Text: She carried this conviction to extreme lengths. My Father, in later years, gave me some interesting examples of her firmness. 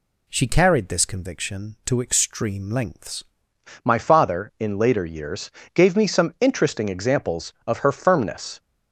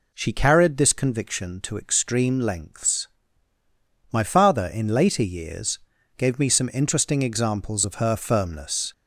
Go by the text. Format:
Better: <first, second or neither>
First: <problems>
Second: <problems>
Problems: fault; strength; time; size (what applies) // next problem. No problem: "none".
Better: second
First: changes voice at "My"; from 3.8 s on; 4.7 s long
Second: none